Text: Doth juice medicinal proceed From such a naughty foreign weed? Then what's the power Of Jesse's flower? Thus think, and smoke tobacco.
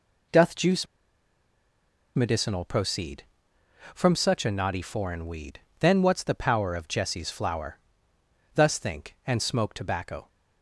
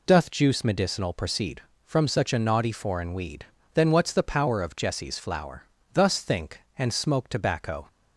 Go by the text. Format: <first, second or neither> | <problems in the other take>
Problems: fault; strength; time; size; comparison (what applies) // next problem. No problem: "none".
second | pauses between "juice" and "medicinal"; strong; at 0.8 s; 1.2 s long